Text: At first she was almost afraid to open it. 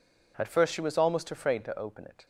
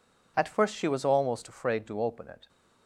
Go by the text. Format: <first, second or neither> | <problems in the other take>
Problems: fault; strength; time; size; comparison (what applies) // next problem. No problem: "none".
neither | none